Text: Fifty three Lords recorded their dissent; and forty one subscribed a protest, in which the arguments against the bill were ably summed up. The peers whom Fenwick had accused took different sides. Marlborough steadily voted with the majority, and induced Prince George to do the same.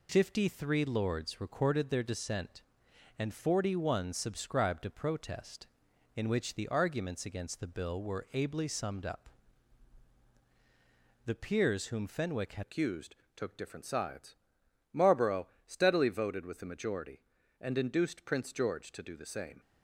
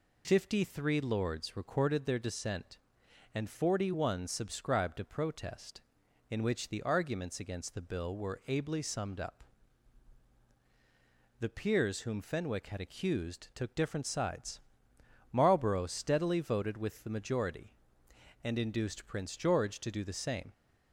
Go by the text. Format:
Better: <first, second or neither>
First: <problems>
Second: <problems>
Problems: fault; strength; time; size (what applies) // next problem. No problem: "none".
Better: second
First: changes voice at "accused"; from 12.6 s on; 6.9 s long // pauses between "accused" and "took"; slight; at 13.1 s; 0.20 s long // pauses between "Marlborough" and "steadily"; slight; at 15.4 s; 0.18 s long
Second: none